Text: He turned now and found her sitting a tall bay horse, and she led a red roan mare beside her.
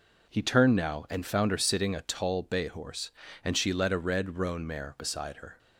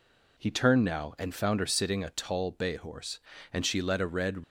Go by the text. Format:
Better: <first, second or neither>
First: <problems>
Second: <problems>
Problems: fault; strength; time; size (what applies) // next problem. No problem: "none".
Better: first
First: none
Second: stops before "roan mare beside her"; at 4.4 s